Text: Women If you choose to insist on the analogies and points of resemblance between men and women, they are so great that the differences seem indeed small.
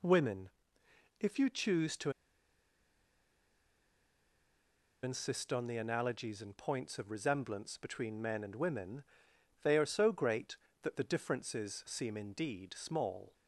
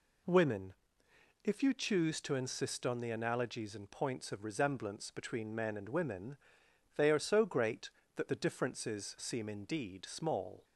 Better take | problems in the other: second | pauses between "Women" and "If"; noticeable; at 0.4 s; 0.72 s long; noticeable in the second // pauses between "to" and "insist"; strong; at 2.1 s; 2.9 s long

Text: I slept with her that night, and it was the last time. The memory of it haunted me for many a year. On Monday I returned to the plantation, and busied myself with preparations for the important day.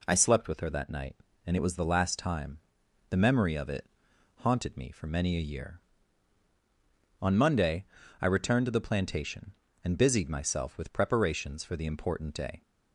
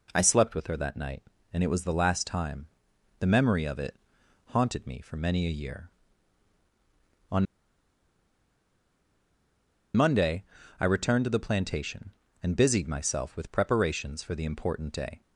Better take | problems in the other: first | pauses between "it" and "haunted"; noticeable; at 3.9 s; 0.48 s long; noticeable in the first // pauses between "On" and "Monday"; strong; at 7.4 s; 2.5 s long // pauses between "Monday" and "I"; at 10.4 s; 0.38 s long; also in the first

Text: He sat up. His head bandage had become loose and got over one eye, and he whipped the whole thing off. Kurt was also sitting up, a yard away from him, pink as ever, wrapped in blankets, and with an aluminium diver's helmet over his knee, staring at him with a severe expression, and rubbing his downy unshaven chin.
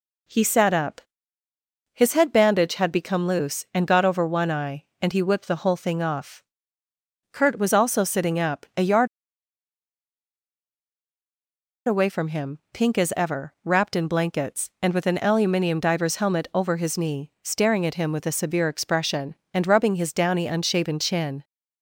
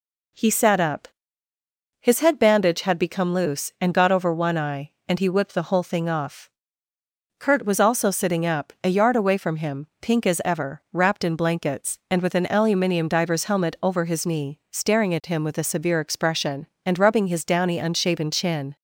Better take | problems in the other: second | pauses between "yard" and "away"; strong; at 9.0 s; 2.8 s long

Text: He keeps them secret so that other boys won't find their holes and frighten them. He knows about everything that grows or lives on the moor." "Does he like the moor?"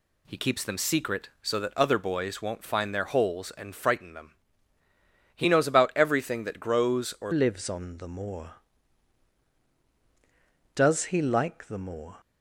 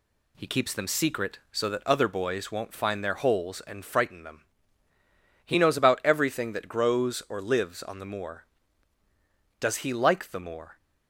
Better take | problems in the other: second | changes voice at "lives"; from 7.3 s on; 4.8 s long

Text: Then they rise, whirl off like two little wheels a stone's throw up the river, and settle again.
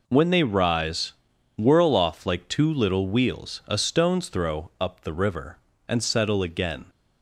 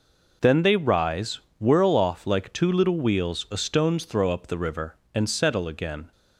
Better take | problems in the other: second | says "When" for "Then"; at 0.0 s

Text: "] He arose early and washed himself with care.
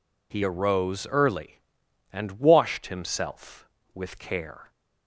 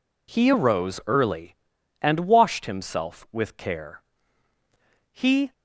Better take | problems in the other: first | goes on to say "He"; slight; from 5.1 s on; 0.42 s long

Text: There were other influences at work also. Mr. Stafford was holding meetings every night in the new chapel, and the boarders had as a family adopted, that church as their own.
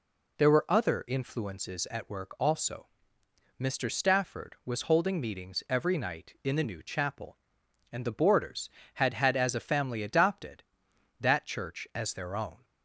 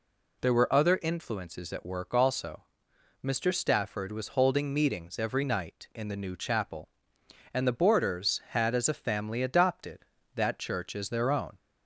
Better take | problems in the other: second | says "had" twice; at 9.1 s

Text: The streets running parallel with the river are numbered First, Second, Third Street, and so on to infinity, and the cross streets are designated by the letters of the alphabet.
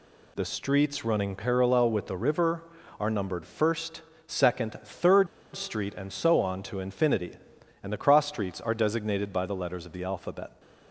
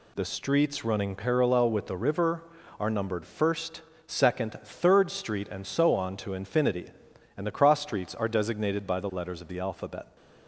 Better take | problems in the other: second | pauses between "Third" and "Street"; slight; at 5.2 s; 0.28 s long

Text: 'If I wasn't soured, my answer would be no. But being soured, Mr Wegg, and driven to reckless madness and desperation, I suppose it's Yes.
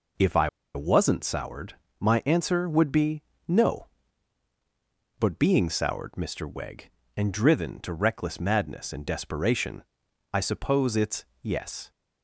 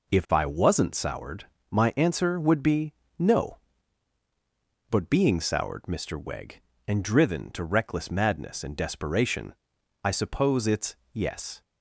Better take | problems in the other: second | pauses between "I" and "wasn't"; slight; at 0.4 s; 0.25 s long // pauses between "be" and "no"; slight; at 3.2 s; 0.26 s long; slight in the second // pauses between "it's" and "Yes"; slight; at 11.2 s; 0.18 s long; slight in the second

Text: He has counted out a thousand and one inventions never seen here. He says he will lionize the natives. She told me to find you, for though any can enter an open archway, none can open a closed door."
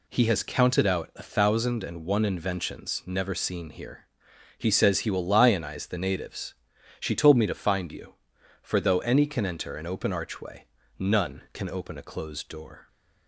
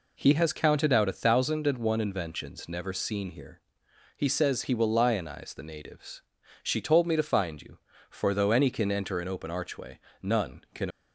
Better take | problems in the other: first | stops before "open a closed door"; at 10.9 s

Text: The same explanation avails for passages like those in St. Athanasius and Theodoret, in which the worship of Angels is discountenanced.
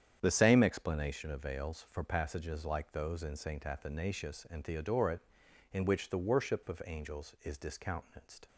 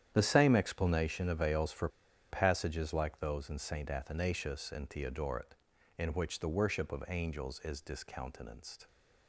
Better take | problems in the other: first | starts louder than the rest; strong; until 1.1 s; 10 dB; strong in the first // pauses between "for" and "passages"; at 1.8 s; 0.42 s long

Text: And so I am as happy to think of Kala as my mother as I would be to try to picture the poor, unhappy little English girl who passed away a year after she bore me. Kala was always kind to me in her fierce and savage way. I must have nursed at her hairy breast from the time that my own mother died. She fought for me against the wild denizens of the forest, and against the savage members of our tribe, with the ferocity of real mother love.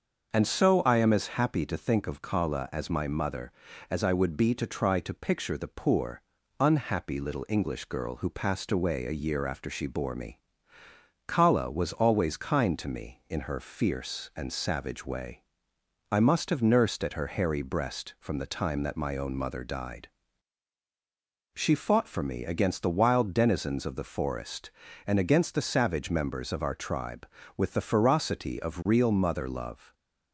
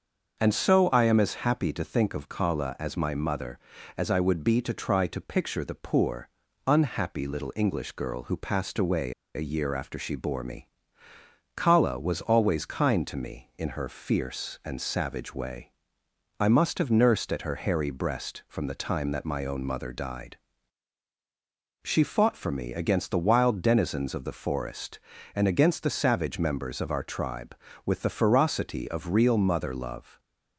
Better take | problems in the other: first | starts louder than the rest; until 1.4 s; 6.5 dB; also in the first // pauses between "away" and "a"; slight; at 9.1 s; 0.23 s long

